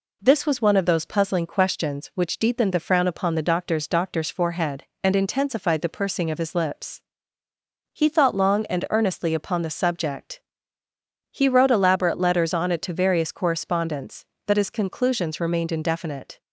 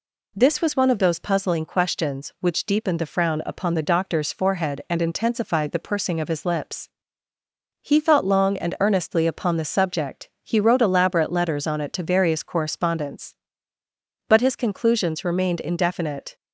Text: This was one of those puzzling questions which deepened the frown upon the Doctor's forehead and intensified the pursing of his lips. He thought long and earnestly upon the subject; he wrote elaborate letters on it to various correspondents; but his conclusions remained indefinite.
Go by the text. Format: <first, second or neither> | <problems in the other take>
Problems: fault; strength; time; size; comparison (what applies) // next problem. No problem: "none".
second | says "Doctor's" twice; at 3.8 s